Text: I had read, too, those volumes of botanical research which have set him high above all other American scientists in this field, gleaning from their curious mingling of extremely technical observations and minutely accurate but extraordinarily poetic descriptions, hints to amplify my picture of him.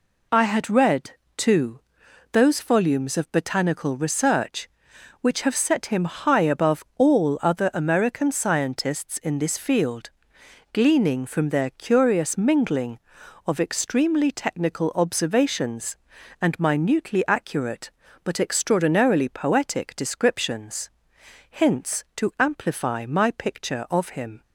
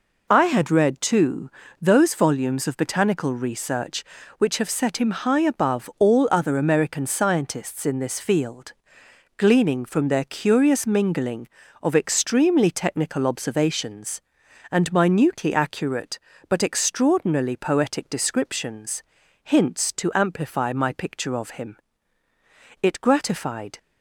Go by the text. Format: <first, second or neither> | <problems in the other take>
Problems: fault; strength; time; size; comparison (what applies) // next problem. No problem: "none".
first | goes on to say "It gratified"; noticeable; from 22.8 s on; 0.96 s long